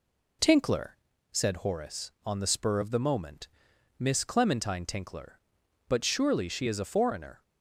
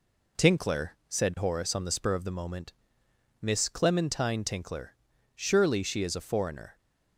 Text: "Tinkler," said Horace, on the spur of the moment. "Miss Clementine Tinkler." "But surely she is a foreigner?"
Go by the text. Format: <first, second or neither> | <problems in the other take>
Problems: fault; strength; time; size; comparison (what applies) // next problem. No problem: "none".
first | skips "But"; at 5.1 s